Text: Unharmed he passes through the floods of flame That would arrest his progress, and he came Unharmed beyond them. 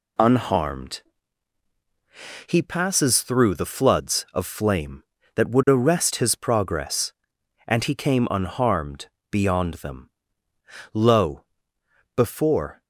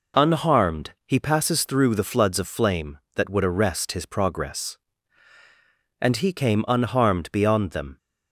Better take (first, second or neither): second